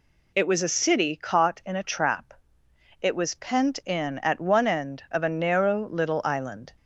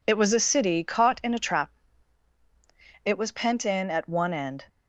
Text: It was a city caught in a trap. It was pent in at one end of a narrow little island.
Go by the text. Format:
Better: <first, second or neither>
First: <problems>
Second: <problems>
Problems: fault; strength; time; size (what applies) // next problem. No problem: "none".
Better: first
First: none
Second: stops before "of a narrow little island"; at 4.6 s